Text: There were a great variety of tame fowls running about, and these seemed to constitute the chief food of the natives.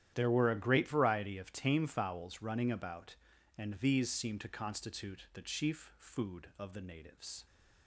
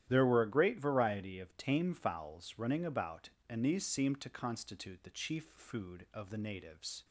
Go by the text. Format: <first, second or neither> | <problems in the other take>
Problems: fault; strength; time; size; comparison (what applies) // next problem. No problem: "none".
neither | starts louder than the rest; strong; the same in both